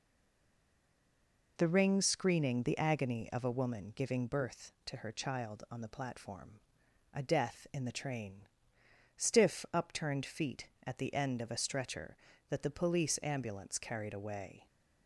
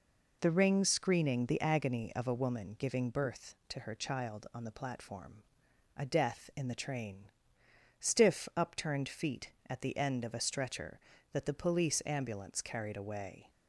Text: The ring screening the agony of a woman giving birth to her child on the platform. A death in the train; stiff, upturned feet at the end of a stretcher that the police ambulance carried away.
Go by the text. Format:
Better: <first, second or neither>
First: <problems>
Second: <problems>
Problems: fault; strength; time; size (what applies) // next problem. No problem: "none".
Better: second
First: stays silent before the first word; noticeable; until 1.5 s; 1.5 s long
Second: none